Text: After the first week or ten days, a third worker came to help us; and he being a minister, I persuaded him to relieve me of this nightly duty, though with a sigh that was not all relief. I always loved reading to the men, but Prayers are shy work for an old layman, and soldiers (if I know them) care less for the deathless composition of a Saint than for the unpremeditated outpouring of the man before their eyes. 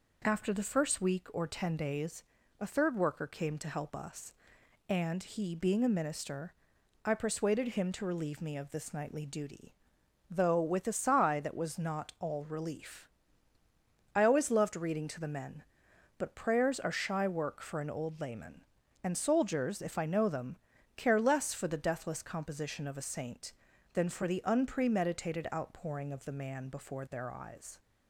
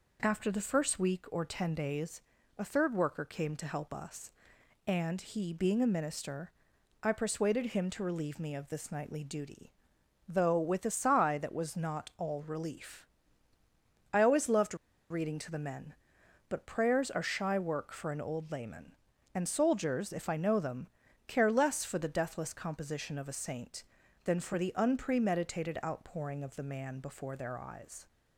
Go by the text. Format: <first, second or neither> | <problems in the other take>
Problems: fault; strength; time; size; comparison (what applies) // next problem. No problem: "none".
first | pauses between "loved" and "reading"; slight; at 14.7 s; 0.35 s long